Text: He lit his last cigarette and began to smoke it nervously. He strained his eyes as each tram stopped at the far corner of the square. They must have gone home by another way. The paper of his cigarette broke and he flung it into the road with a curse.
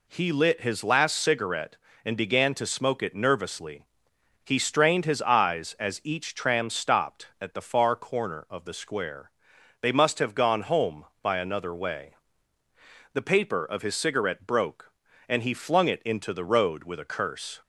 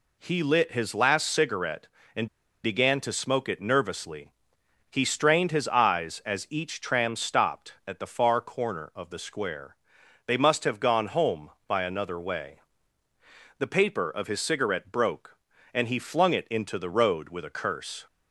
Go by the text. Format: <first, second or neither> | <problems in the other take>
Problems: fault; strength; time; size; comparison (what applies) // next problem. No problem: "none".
first | pauses between "and" and "began"; at 2.2 s; 0.37 s long